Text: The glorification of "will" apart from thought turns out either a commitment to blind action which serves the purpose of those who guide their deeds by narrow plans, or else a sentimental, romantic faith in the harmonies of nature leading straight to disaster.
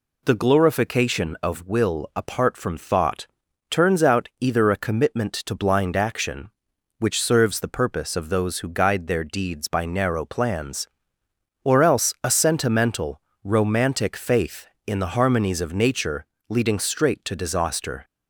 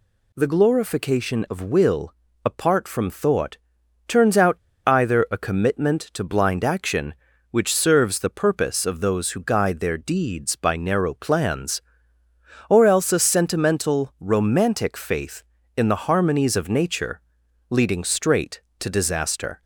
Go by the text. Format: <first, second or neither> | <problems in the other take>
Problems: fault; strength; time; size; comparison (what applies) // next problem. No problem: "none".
first | pauses between "will" and "apart"; slight; at 2.1 s; 0.28 s long // pauses between "thought" and "turns"; noticeable; at 3.5 s; 0.50 s long; also in the first // pauses between "out" and "either"; slight; at 4.5 s; 0.31 s long // pauses between "nature" and "leading"; noticeable; at 17.2 s; 0.48 s long; slight in the first